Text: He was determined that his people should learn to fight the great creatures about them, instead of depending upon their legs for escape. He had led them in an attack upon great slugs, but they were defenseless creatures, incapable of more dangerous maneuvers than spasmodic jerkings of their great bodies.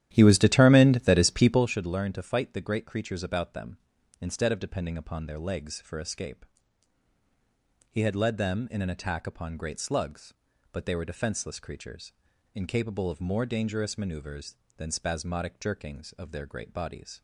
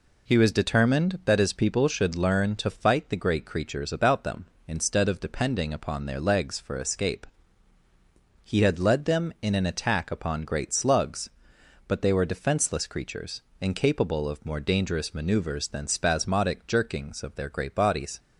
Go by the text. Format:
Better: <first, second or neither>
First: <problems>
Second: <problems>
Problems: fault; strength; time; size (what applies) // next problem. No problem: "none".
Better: second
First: starts louder than the rest; strong; until 1.7 s; 12 dB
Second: none